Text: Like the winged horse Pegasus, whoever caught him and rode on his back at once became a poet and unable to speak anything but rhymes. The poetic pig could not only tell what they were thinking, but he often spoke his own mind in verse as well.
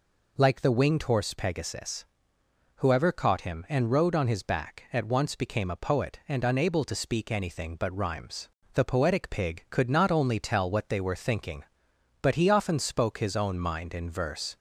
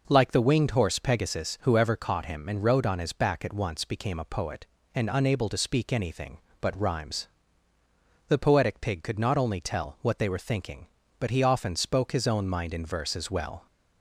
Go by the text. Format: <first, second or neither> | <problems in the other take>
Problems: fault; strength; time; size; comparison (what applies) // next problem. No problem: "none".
second | stops before "as well"; at 14.5 s